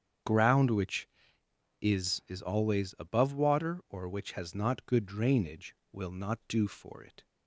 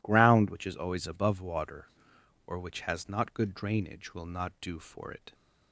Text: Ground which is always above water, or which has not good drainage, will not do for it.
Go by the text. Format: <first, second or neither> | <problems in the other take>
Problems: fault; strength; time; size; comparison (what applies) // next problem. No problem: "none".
second | starts louder than the rest; strong; until 1.9 s; 8 dB // says "is" twice; at 2.2 s